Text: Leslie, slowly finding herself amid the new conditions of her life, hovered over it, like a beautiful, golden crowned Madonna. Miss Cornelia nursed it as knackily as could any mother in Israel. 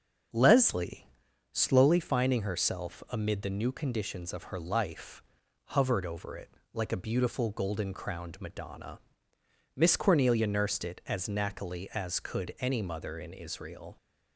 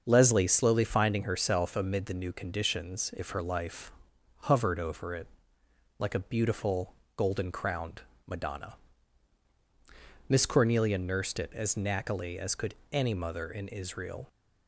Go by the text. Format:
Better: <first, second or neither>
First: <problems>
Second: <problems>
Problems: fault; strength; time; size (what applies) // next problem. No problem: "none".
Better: first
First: starts louder than the rest; until 1.7 s; 6.5 dB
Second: starts louder than the rest; until 1.0 s; 6.5 dB // says "if" for "of"; at 3.1 s // pauses between "crowned" and "Madonna"; slight; at 8.0 s; 0.24 s long // pauses between "could" and "any"; slight; at 12.7 s; 0.16 s long